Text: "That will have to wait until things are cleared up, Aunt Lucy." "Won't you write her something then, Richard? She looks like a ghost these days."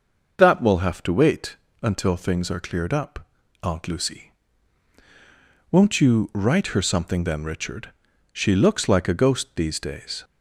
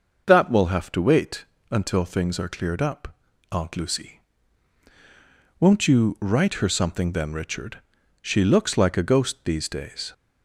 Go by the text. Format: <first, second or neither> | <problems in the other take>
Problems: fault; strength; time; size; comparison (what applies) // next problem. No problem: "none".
neither | pauses between "wait" and "until"; slight; the same in both